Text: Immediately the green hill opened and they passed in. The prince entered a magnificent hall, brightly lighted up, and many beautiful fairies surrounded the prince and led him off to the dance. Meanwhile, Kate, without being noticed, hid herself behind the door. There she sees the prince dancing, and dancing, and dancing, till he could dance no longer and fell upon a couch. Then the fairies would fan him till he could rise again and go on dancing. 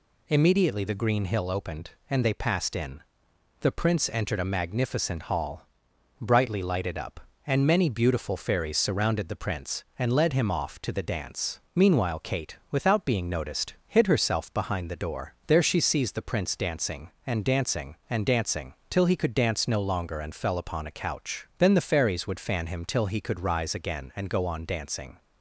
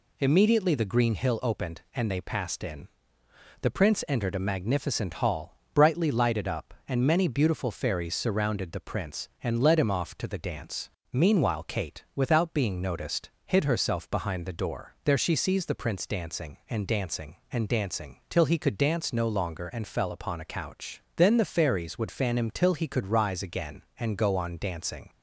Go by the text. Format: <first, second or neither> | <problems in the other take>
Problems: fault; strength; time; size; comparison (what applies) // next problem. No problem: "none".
neither | none